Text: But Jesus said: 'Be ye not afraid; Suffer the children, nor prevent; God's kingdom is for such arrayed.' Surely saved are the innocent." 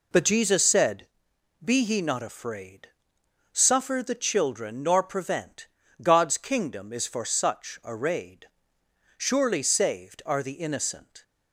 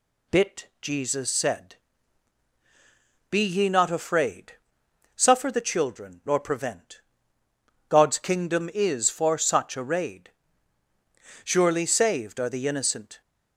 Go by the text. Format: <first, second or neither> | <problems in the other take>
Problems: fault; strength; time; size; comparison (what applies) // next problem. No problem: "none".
first | says "Bit" for "But"; at 0.3 s